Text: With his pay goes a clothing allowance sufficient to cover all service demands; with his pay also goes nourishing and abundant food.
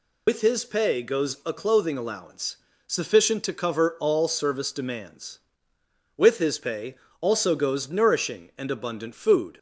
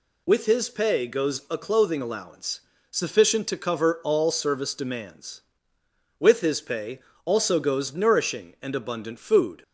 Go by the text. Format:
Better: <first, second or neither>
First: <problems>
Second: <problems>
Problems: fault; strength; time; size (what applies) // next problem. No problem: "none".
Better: second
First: loses the start of "With"; at 0.2 s; 60 ms // pauses between "allowance" and "sufficient"; slight; at 2.5 s; 0.30 s long // pauses between "pay" and "also"; slight; at 6.9 s; 0.24 s long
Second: pauses between "allowance" and "sufficient"; slight; at 2.6 s; 0.30 s long // pauses between "pay" and "also"; slight; at 6.9 s; 0.24 s long